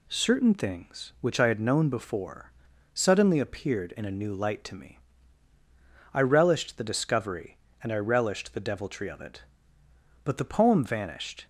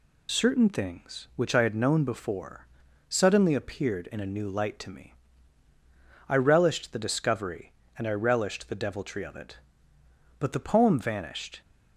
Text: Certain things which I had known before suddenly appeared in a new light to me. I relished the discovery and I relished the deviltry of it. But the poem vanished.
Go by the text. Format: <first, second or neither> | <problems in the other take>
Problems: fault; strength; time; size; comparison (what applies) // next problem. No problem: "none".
first | loses the start of "Certain"; at 0.2 s; 65 ms // pauses between "before" and "suddenly"; at 2.6 s; 0.42 s long; also in the first